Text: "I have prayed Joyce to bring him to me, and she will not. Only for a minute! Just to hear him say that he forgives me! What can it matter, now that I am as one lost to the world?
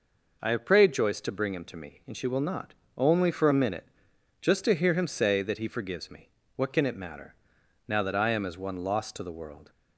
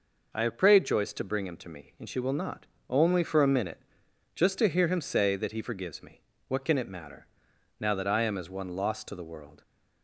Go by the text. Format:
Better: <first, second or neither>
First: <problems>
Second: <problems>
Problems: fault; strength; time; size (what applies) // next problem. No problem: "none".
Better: neither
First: none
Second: none